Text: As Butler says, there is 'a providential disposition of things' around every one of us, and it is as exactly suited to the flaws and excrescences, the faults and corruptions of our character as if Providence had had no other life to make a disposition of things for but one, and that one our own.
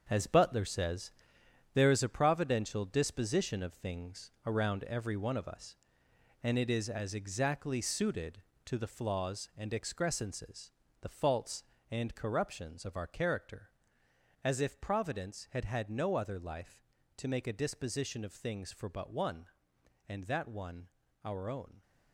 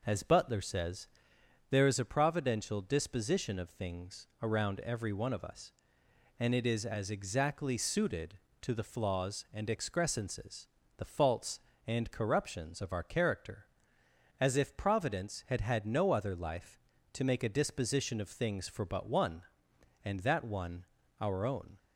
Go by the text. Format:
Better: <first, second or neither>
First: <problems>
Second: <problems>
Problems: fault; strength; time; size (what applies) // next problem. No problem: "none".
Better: second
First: gets quieter; strong; throughout; 8.5 dB // pauses between "one" and "our"; slight; at 20.8 s; 0.34 s long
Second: pauses between "one" and "our"; slight; at 20.8 s; 0.34 s long